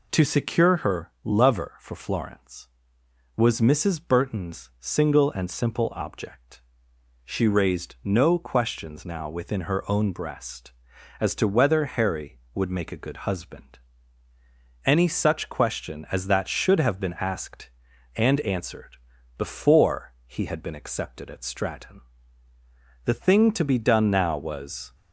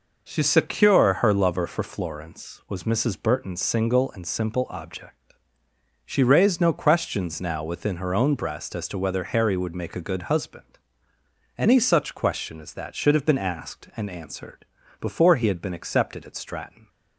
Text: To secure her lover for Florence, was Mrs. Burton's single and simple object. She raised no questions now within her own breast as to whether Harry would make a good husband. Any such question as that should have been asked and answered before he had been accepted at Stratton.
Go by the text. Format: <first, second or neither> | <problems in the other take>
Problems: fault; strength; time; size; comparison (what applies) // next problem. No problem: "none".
second | pauses between "answered" and "before"; at 18.9 s; 0.40 s long; slight in the second // goes on to say "The thing to be done now was"; strong; from 23.0 s on; 1.9 s long